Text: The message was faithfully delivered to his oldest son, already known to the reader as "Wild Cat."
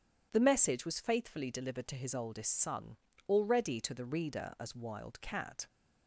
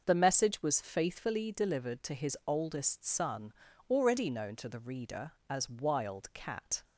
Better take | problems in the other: second | skips "known"; at 3.7 s

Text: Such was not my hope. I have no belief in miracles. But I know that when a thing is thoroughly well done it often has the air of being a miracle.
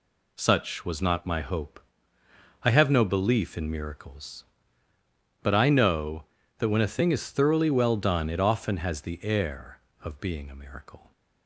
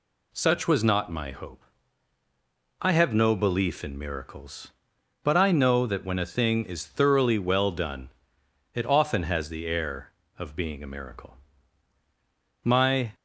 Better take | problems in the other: first | pauses between "done" and "it"; noticeable; at 8.0 s; 0.64 s long // goes on to say "My"; slight; from 12.6 s on; 0.48 s long

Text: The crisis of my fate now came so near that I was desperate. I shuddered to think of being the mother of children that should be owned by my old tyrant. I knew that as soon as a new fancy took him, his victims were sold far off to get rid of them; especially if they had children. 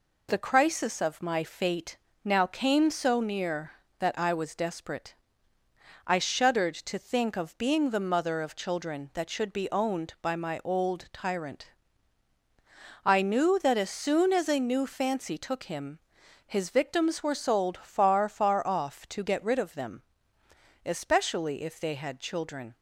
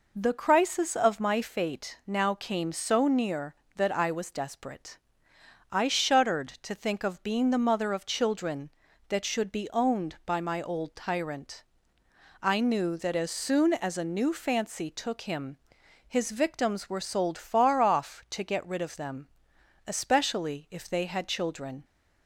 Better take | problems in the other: second | pauses between "fate" and "now"; slight; at 1.9 s; 0.26 s long // says "far" twice; at 18.2 s

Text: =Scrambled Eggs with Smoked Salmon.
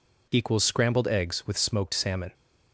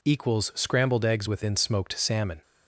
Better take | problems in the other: first | says "within" for "with"; at 1.2 s

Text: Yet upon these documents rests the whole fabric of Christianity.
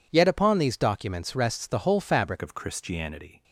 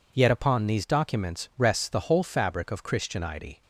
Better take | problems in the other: second | changes voice at "of"; from 2.4 s on; 1.0 s long

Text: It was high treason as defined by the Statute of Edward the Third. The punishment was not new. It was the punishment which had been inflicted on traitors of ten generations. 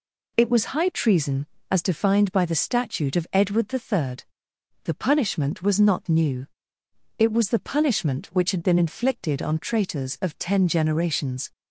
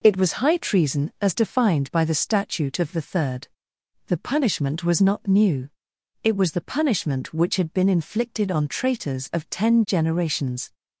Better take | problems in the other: first | skips "Edward"; at 2.9 s

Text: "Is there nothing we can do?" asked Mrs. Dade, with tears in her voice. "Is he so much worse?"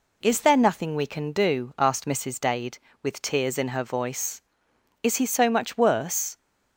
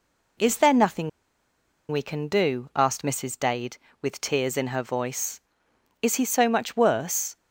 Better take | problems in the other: first | pauses between "nothing" and "we"; noticeable; at 1.0 s; 0.80 s long

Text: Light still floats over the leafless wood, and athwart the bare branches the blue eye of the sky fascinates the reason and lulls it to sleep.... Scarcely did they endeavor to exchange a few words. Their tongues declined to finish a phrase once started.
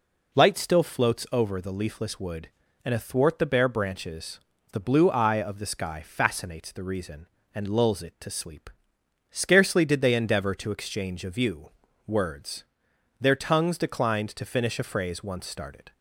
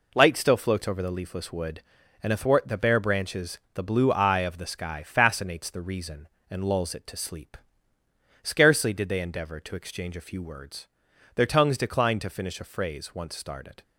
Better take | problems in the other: second | pauses between "branches" and "the"; slight; at 4.4 s; 0.32 s long; slight in the second // says "view" for "few"; at 11.3 s

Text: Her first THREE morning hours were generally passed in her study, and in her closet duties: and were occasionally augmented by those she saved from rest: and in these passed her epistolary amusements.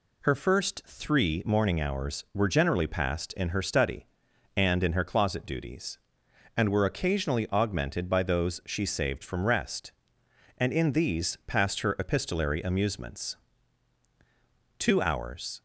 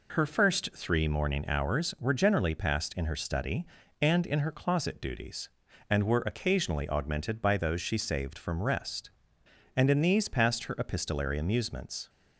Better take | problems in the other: second | goes on to say "Two hours"; noticeable; from 14.7 s on; 0.84 s long

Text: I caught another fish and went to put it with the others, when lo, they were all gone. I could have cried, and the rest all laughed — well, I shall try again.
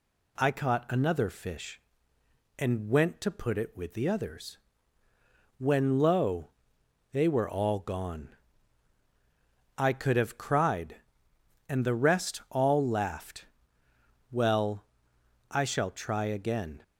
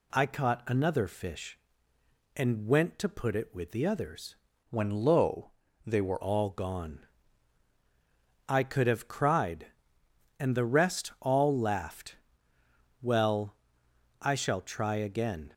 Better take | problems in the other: first | changes voice from "when" to "were"; from 4.6 to 6.2 s; 1.6 s long

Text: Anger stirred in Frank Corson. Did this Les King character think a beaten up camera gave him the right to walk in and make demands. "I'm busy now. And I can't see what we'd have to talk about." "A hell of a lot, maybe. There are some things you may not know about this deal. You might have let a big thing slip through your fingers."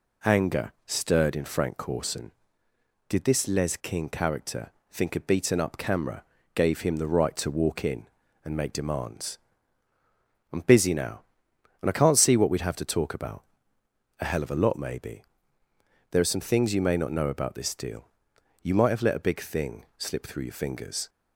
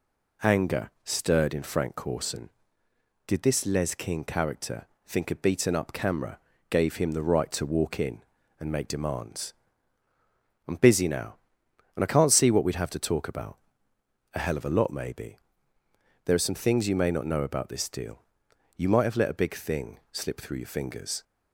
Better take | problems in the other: neither | pauses between "character" and "think"; slight; the same in both // pauses between "camera" and "gave"; slight; the same in both

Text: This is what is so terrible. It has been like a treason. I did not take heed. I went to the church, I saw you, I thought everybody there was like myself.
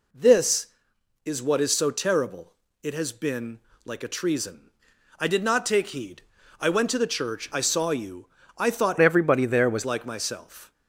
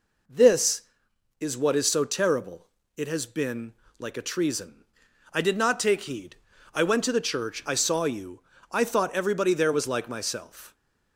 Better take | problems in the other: second | pauses between "been" and "like"; slight; at 3.5 s; 0.26 s long; slight in the second // changes voice from "everybody" to "was"; from 9.0 to 9.8 s; 0.8 s long

